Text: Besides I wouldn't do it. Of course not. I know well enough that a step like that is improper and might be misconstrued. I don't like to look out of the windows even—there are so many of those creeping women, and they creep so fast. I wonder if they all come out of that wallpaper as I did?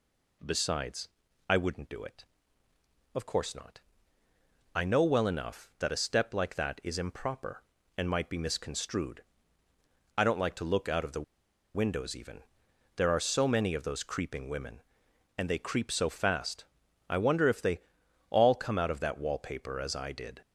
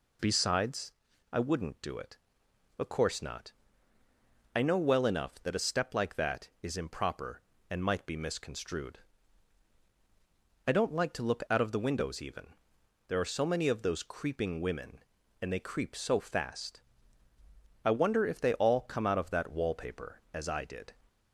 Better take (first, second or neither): second